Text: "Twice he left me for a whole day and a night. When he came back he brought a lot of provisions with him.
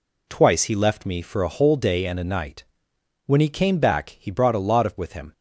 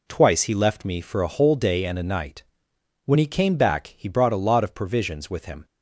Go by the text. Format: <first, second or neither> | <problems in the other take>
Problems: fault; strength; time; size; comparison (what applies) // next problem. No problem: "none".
second | skips "provisions"; at 4.9 s